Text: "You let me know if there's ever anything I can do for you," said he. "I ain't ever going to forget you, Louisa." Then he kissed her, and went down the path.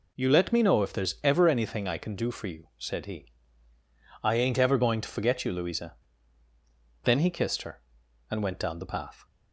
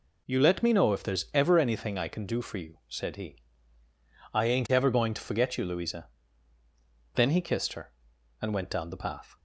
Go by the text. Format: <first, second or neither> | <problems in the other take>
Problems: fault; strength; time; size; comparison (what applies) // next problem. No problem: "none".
neither | none